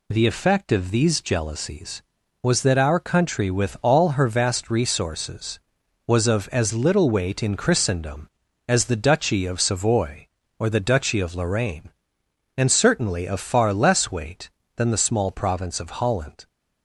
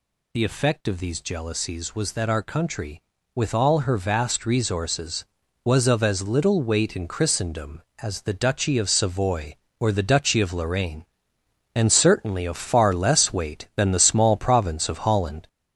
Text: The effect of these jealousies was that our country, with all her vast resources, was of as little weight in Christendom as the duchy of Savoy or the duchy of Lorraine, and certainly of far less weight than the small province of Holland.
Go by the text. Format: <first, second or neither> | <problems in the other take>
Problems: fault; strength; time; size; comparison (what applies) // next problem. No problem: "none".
first | gets louder; noticeable; throughout; 4 dB